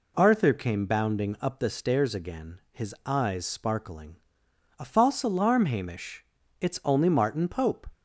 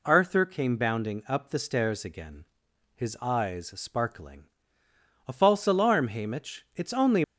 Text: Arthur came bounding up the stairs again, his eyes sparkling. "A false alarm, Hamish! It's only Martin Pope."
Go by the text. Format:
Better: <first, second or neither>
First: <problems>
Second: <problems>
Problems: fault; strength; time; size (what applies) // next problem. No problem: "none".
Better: first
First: none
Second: stops before "Martin Pope"; at 7.2 s